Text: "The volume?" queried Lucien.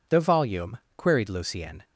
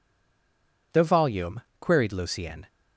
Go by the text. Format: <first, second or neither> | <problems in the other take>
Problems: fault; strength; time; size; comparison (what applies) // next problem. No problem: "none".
first | stays silent before the first word; slight; until 0.9 s; 0.9 s long